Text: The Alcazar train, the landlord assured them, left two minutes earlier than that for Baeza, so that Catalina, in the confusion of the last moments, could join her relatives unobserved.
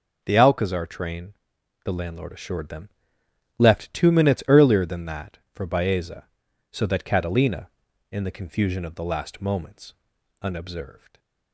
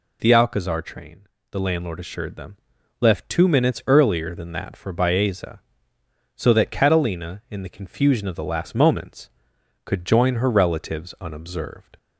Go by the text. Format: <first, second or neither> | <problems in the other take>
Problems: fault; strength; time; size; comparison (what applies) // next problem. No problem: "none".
second | skips "could join her relatives"; at 10.1 s // stays silent after the last word; slight; from 10.9 s on; 0.6 s long